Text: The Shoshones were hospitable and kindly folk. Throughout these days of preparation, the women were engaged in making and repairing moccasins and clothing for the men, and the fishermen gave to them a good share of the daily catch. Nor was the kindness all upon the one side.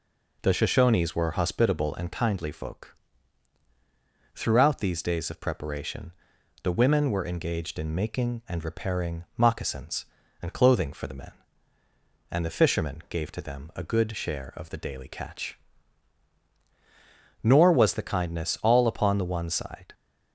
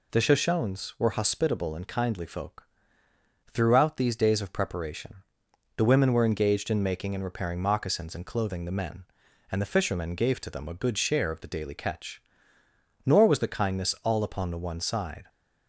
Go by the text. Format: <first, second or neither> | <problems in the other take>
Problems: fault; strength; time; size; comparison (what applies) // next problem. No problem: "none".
first | skips "for"; at 8.6 s